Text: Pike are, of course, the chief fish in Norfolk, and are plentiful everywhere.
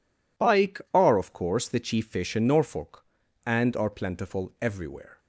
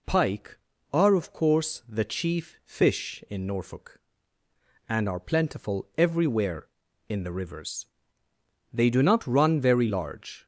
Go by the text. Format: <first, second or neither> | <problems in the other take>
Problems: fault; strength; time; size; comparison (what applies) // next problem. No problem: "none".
first | goes on to say "In the rivers they do not run very large"; strong; from 7.0 s on; 3.3 s long